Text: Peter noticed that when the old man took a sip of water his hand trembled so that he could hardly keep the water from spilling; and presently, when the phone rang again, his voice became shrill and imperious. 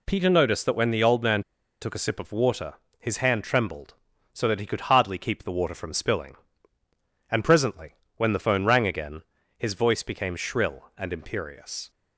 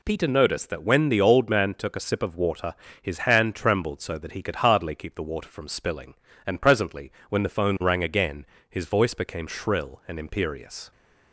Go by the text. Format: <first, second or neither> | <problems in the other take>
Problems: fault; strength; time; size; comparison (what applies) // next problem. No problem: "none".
second | pauses between "man" and "took"; at 1.4 s; 0.39 s long // pauses between "water" and "his"; slight; at 2.7 s; 0.24 s long; slight in the second